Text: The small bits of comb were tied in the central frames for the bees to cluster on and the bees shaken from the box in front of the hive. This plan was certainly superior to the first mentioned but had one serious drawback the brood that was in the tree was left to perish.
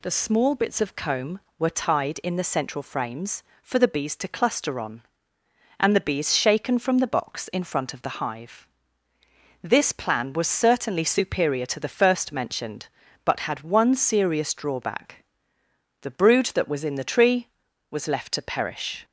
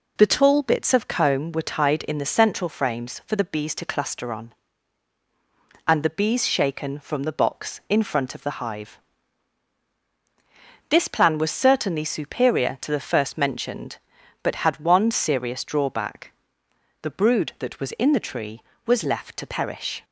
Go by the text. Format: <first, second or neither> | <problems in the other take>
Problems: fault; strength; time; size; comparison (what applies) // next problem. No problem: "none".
first | says "tall" for "small"; at 0.2 s // pauses between "drawback" and "the"; noticeable; at 16.3 s; 0.70 s long; noticeable in the first